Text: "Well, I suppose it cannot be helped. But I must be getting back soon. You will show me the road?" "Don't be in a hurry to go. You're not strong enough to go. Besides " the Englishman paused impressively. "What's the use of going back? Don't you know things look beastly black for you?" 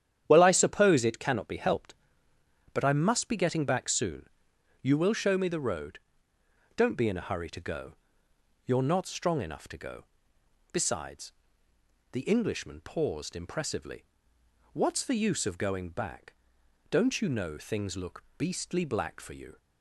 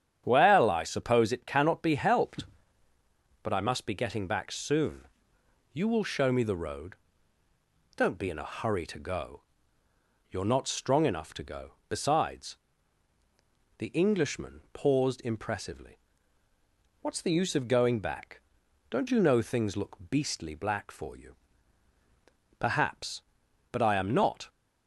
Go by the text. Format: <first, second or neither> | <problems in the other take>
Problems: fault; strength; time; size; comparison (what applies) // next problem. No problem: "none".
first | starts louder than the rest; strong; until 1.2 s; 9.5 dB; strong in the first // goes on to say "Perhaps but I am not"; strong; from 22.5 s on; 1.9 s long